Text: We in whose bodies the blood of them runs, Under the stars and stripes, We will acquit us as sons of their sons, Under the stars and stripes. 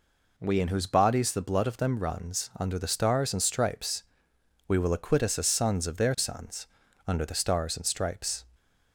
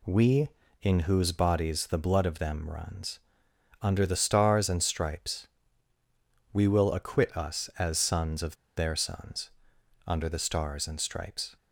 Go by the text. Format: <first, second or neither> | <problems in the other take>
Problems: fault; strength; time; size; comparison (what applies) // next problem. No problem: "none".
first | pauses between "of" and "their"; slight; at 8.5 s; 0.21 s long